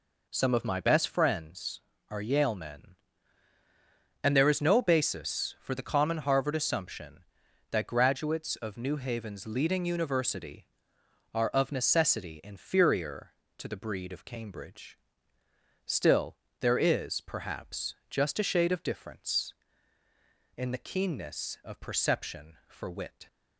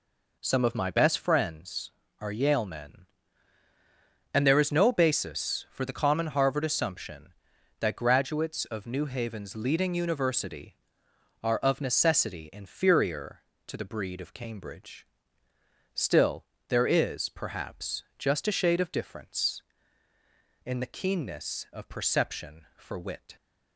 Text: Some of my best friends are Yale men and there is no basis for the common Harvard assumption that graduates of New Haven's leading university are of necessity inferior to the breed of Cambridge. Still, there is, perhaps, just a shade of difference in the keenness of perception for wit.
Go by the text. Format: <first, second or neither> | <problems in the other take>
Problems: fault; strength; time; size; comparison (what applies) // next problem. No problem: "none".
neither | none